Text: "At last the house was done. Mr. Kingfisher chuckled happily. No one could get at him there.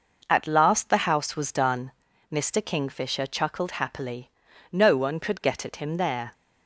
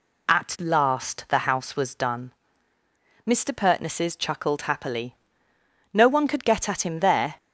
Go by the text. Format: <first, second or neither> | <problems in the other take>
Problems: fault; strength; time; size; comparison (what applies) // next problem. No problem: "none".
first | says "Pertnesses" for "Kingfisher"; at 3.5 s